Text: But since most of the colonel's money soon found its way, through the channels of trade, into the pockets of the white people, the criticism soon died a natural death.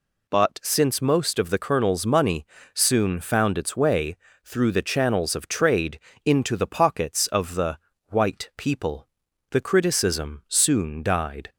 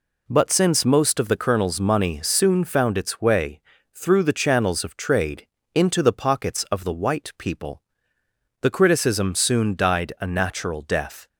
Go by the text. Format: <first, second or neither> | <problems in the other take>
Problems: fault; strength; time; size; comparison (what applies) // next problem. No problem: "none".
second | pauses between "money" and "soon"; slight; at 2.4 s; 0.28 s long // pauses between "the" and "white"; slight; at 7.7 s; 0.32 s long // stops before "a natural death"; at 11.5 s